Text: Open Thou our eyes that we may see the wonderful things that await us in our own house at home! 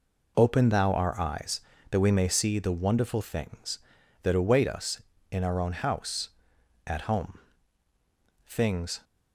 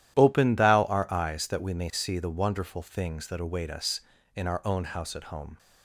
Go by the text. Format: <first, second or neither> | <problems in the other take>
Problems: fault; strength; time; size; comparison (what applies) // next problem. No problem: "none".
second | goes on to say "Things"; from 8.4 s on; 0.60 s long